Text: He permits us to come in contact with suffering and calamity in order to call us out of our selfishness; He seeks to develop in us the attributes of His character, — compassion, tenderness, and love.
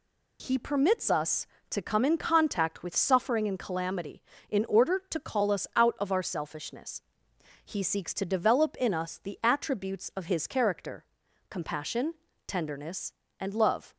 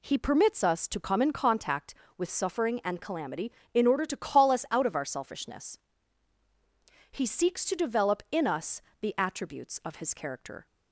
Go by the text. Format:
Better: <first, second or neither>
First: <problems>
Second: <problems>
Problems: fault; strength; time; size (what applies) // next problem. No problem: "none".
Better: first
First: none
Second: pauses between "us" and "the"; slight; at 8.8 s; 0.20 s long // stops before "compassion tenderness and love"; at 10.6 s